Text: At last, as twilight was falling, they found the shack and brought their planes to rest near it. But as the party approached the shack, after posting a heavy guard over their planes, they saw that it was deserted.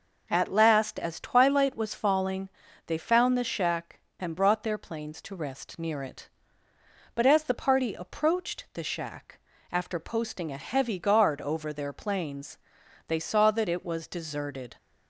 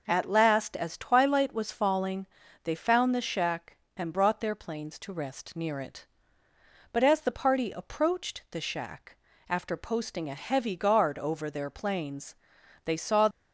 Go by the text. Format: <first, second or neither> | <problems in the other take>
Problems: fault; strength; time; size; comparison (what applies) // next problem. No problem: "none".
first | stops before "that it was deserted"; at 13.2 s